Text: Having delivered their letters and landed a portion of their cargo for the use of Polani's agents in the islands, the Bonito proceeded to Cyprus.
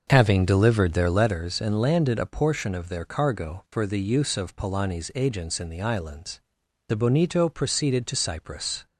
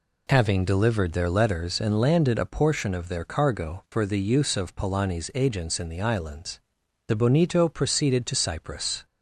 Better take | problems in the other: second | starts louder than the rest; until 1.4 s; 6.5 dB

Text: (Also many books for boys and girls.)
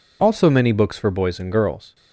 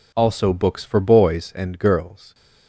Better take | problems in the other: first | skips "many"; at 0.5 s

